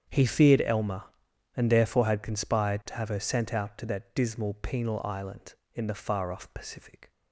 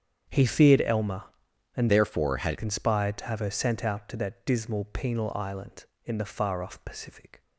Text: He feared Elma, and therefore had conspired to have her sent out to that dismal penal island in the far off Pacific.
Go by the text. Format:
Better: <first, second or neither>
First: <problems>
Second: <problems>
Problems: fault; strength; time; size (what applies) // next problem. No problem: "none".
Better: first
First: starts louder than the rest; strong; until 1.5 s; 8 dB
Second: starts louder than the rest; strong; until 1.7 s; 8 dB // changes voice from "therefore" to "had"; from 1.8 to 2.5 s; 0.7 s long